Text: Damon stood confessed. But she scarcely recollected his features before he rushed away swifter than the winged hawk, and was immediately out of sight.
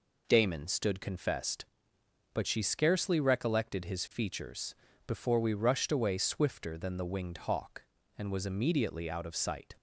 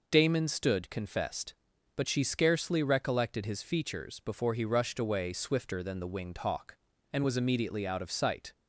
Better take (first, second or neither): second